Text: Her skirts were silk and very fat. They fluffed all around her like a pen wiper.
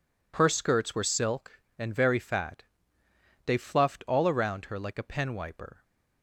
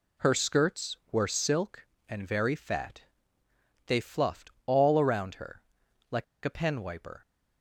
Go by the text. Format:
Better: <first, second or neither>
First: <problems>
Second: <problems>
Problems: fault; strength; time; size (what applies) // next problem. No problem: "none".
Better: first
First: none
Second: pauses between "fluffed" and "all"; slight; at 4.4 s; 0.16 s long // pauses between "her" and "like"; noticeable; at 5.6 s; 0.48 s long // pauses between "like" and "a"; slight; at 6.2 s; 0.20 s long